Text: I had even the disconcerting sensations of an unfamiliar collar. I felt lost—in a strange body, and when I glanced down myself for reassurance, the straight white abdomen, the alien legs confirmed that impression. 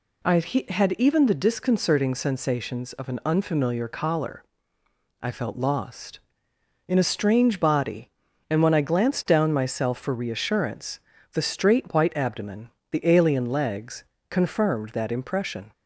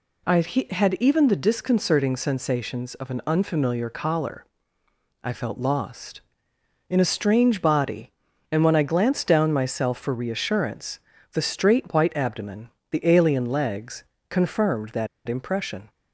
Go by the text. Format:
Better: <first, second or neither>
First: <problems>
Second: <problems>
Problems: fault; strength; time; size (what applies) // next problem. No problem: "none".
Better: first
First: pauses between "legs" and "confirmed"; slight; at 14.0 s; 0.26 s long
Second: pauses between "legs" and "confirmed"; slight; at 14.0 s; 0.26 s long // pauses between "that" and "impression"; slight; at 15.0 s; 0.19 s long